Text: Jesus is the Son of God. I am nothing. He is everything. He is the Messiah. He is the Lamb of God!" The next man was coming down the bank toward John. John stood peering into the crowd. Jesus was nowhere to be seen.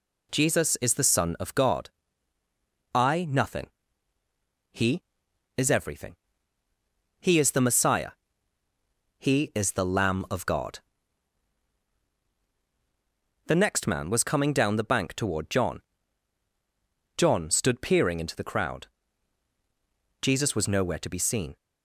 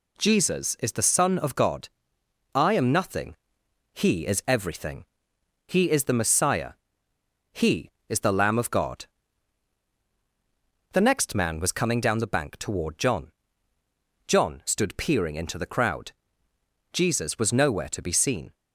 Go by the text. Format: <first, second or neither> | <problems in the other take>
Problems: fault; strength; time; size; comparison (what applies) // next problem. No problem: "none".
second | skips "am"; at 3.2 s